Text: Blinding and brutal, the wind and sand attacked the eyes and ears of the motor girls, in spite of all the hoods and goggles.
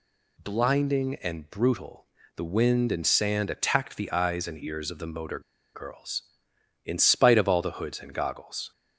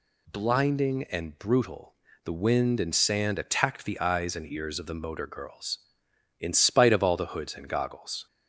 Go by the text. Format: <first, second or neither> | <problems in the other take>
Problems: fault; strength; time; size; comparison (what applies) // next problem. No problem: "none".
second | pauses between "motor" and "girls"; slight; at 5.3 s; 0.34 s long